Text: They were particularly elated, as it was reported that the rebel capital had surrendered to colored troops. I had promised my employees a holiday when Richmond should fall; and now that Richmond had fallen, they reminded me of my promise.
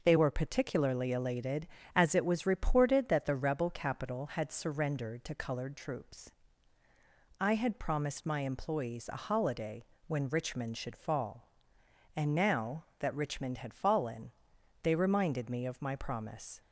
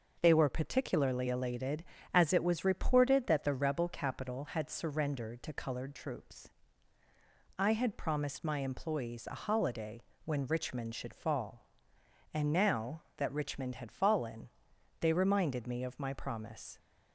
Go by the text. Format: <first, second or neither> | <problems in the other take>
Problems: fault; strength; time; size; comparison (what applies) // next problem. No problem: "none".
neither | pauses between "holiday" and "when"; slight; the same in both